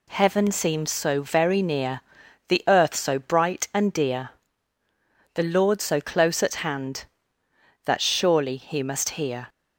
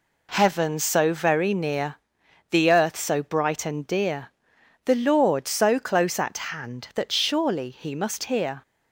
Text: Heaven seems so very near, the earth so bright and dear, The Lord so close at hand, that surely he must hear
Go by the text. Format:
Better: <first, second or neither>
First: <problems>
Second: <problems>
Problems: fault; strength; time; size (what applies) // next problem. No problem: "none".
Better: first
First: none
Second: skips "seems"; at 0.7 s // pauses between "at" and "hand"; slight; at 6.3 s; 0.16 s long